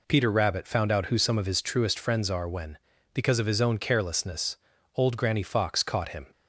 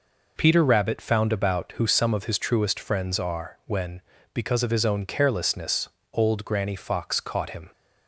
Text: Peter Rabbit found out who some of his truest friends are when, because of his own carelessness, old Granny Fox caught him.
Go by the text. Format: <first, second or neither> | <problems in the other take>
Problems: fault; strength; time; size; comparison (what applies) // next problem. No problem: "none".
first | says "about" for "out"; at 1.3 s